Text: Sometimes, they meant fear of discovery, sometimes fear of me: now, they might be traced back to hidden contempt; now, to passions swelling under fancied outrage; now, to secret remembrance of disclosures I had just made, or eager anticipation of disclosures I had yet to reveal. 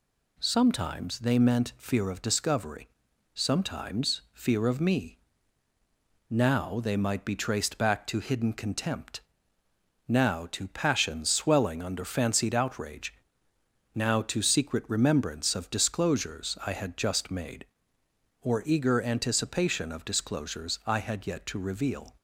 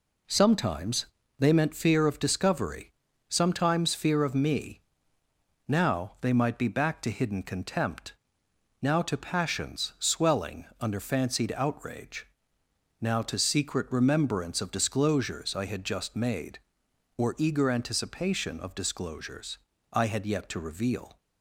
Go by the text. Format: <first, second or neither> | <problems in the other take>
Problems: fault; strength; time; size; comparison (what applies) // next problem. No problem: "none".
first | skips "traced"; at 6.6 s // pauses between "swelling" and "under"; slight; at 10.6 s; 0.16 s long // pauses between "disclosures" and "I"; slight; at 19.5 s; 0.34 s long